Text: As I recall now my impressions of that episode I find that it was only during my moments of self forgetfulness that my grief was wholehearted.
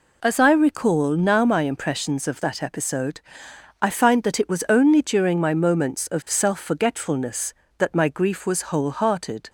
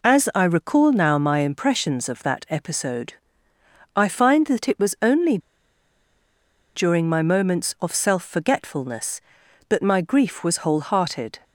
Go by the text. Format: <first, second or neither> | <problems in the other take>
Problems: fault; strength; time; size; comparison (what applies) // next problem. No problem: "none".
first | pauses between "episode" and "I"; noticeable; at 3.1 s; 0.80 s long; noticeable in the first // pauses between "only" and "during"; strong; at 5.3 s; 1.3 s long